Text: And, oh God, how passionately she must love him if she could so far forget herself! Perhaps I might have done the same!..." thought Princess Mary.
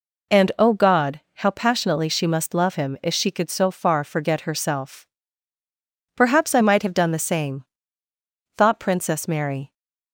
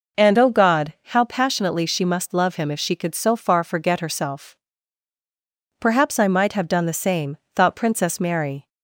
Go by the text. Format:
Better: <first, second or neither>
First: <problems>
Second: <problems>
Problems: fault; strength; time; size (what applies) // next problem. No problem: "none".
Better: neither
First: none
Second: none